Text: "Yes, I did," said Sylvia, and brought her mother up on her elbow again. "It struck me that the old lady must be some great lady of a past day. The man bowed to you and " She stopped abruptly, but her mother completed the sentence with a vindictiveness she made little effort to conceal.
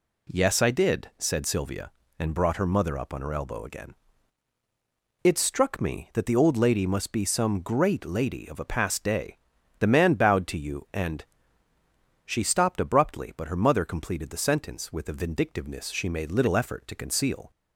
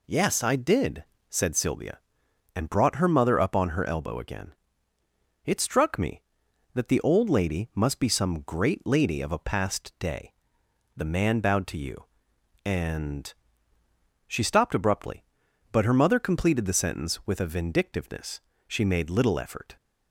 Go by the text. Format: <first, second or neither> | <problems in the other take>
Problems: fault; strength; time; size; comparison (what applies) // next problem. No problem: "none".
first | pauses between "vindictiveness" and "she"; slight; at 18.3 s; 0.28 s long // stops before "to conceal"; at 19.7 s